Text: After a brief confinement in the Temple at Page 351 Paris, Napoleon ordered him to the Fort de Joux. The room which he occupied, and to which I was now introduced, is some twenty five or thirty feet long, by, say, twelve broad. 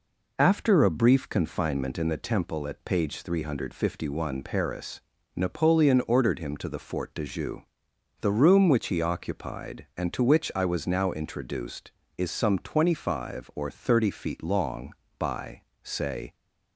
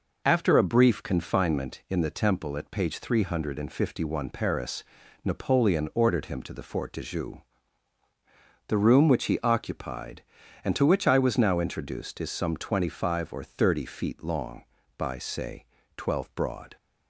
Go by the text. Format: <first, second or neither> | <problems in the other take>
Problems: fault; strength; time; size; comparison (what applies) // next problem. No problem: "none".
second | stops before "twelve broad"; at 16.3 s